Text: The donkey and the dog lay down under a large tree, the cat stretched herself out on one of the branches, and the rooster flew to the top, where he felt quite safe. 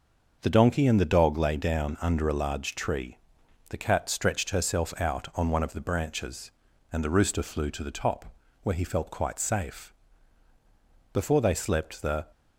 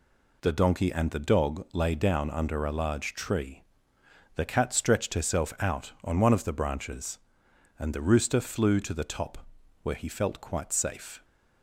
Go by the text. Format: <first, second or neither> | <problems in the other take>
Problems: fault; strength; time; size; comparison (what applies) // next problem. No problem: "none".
second | starts louder than the rest; until 1.4 s; 6 dB // goes on to say "Before they slept the"; noticeable; from 11.1 s on; 1.1 s long